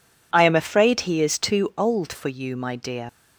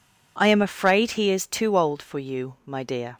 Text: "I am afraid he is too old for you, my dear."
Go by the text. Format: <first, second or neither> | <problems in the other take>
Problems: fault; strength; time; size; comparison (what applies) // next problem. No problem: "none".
second | leaves "dear" unfinished; at 3.0 s; 75 ms